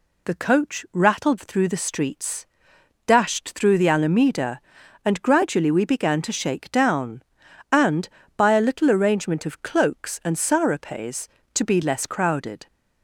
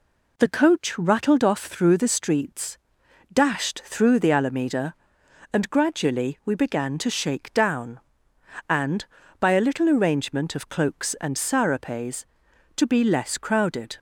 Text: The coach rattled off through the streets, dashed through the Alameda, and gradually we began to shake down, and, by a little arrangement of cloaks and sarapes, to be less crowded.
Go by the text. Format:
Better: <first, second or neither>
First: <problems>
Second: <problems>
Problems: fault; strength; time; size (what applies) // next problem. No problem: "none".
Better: second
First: skips "off"; at 1.3 s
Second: none